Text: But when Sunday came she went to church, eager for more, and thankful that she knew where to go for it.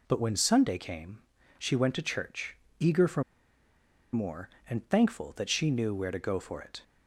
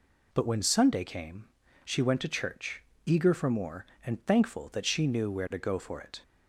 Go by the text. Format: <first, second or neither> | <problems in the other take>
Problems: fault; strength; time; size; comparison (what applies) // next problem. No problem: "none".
second | pauses between "came" and "she"; at 1.1 s; 0.38 s long; also in the second // pauses between "for" and "more"; noticeable; at 3.2 s; 0.89 s long